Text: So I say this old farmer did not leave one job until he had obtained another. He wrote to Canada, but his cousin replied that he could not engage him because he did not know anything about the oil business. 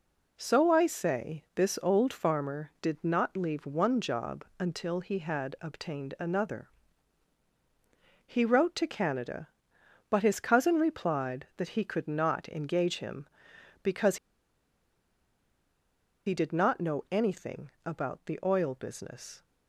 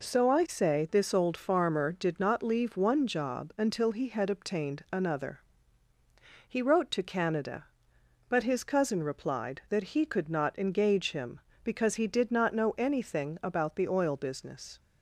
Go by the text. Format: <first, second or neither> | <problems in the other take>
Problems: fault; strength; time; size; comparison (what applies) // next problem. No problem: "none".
second | pauses between "because" and "he"; strong; at 14.1 s; 2.0 s long // pauses between "anything" and "about"; slight; at 17.7 s; 0.16 s long